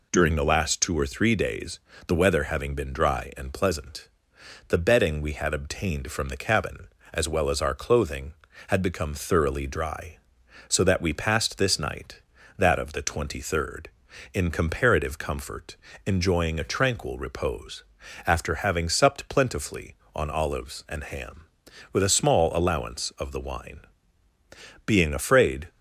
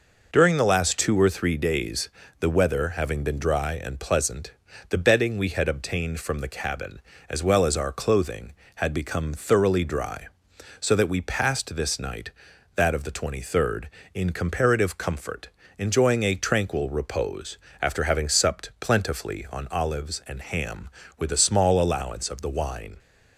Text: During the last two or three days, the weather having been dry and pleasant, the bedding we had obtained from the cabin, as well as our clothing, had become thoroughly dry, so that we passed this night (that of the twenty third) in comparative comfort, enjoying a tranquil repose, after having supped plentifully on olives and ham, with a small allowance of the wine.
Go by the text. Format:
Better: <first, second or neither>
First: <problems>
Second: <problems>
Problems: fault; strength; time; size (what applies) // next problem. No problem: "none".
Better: second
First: goes on to say "Being afraid"; noticeable; from 24.8 s on; 0.82 s long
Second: none